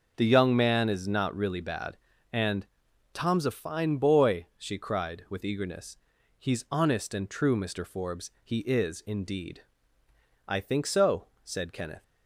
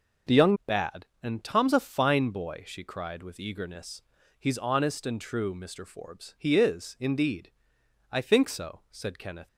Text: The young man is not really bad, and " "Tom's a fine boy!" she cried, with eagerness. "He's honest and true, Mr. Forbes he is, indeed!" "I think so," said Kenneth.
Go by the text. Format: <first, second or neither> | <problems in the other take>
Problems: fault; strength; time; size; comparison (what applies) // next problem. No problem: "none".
first | starts louder than the rest; until 1.6 s; 6 dB // skips "man is not really"; at 0.6 s